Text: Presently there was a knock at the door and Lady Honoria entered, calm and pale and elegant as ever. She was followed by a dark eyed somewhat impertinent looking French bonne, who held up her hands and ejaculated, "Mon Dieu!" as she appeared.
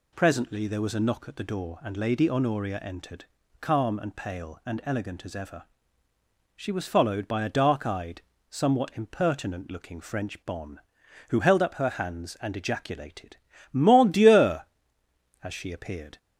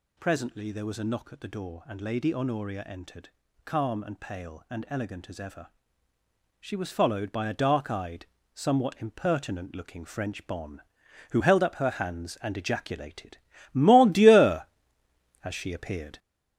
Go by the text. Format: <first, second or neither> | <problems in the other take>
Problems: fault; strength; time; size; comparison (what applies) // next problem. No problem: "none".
first | gets louder; throughout; 6.5 dB // pauses between "eyed" and "somewhat"; slight; at 8.2 s; 0.28 s long; slight in the first